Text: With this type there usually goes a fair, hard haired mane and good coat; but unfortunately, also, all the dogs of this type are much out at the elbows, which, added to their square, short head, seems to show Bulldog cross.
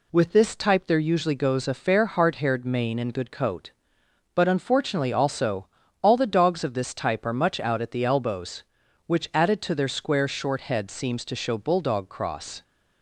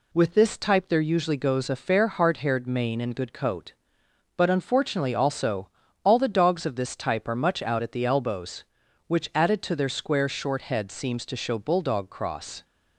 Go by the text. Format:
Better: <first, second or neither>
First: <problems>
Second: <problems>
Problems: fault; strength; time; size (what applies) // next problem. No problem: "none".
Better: neither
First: none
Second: none